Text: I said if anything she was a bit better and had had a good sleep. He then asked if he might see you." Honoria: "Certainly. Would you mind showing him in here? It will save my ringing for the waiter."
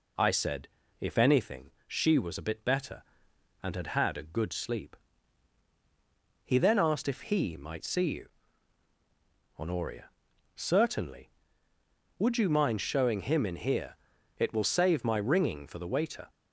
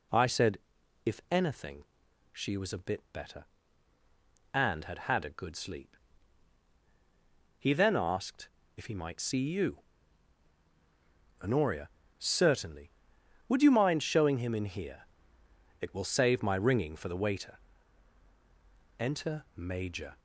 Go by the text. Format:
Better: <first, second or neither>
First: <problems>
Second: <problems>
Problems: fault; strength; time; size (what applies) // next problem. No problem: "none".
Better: first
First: pauses between "said" and "if"; slight; at 0.6 s; 0.32 s long // pauses between "anything" and "she"; slight; at 1.6 s; 0.18 s long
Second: pauses between "said" and "if"; noticeable; at 0.5 s; 0.46 s long // pauses between "anything" and "she"; noticeable; at 1.8 s; 0.48 s long // pauses between "asked" and "if"; slight; at 8.4 s; 0.28 s long // goes on to say "Enter Major"; noticeable; from 18.9 s on; 1.2 s long